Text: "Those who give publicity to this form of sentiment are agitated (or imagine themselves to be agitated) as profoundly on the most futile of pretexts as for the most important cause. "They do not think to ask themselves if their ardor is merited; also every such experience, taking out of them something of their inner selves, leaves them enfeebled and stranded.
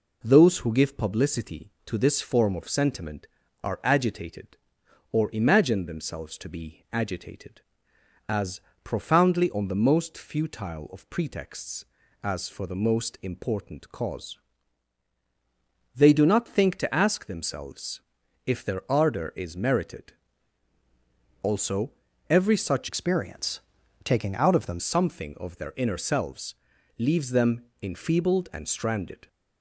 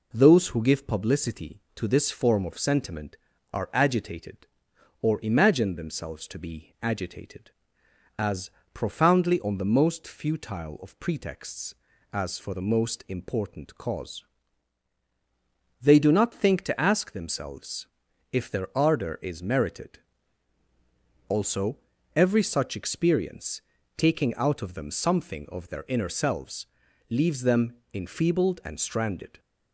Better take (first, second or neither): second